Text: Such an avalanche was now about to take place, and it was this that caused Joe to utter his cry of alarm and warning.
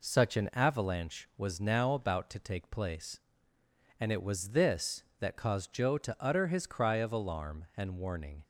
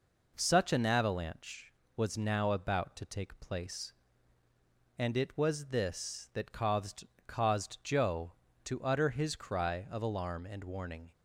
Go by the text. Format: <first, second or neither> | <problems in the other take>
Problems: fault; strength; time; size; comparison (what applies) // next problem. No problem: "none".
first | says "caused" twice; at 7.2 s